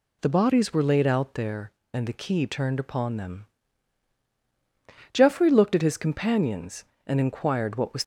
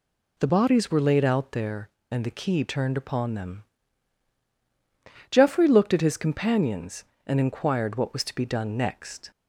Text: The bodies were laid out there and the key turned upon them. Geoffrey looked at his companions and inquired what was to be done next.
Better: second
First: stops before "to be done next"; at 8.0 s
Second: none

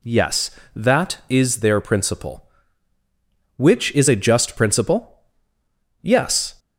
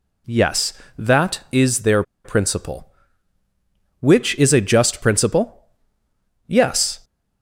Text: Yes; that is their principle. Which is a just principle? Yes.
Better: first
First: none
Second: pauses between "their" and "principle"; slight; at 2.0 s; 0.22 s long

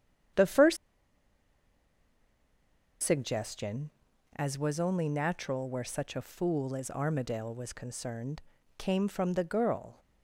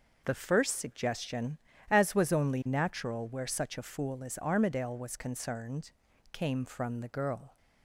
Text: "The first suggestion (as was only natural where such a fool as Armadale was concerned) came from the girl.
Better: second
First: starts louder than the rest; strong; until 3.6 s; 9 dB // pauses between "first" and "suggestion"; strong; at 0.7 s; 2.2 s long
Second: none

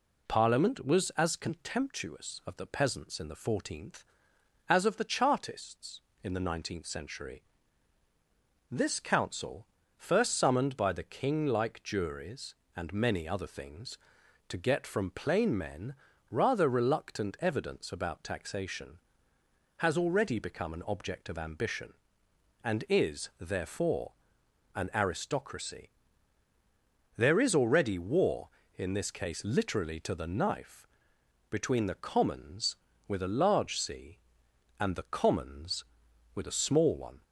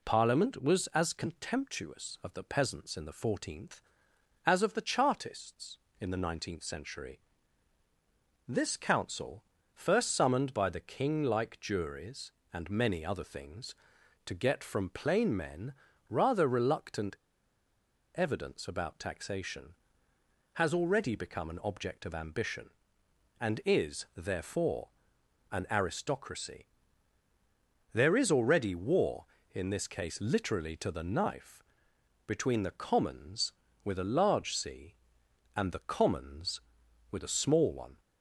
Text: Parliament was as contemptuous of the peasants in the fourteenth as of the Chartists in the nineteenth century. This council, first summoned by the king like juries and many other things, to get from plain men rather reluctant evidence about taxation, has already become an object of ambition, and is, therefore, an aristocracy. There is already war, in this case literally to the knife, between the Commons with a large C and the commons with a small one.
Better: first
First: pauses between "men" and "rather"; slight; at 15.9 s; 0.36 s long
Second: pauses between "men" and "rather"; slight; at 15.7 s; 0.36 s long // pauses between "reluctant" and "evidence"; at 17.1 s; 1.0 s long

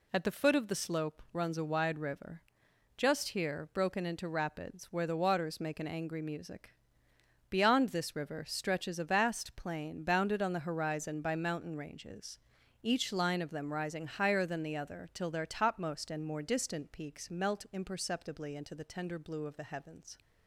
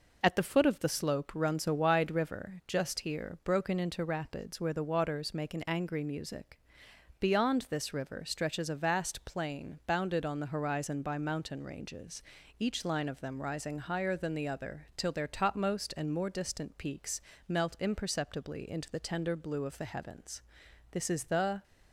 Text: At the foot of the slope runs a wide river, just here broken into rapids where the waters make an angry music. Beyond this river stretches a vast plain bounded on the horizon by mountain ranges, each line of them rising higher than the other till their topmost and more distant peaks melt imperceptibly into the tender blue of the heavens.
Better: first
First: none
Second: pauses between "peaks" and "melt"; slight; at 17.1 s; 0.30 s long // goes on to say "This is the"; noticeable; from 20.9 s on; 0.72 s long

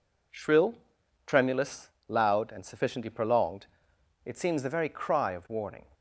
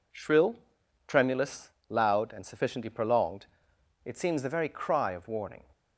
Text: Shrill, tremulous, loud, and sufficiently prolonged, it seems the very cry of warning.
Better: neither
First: none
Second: none

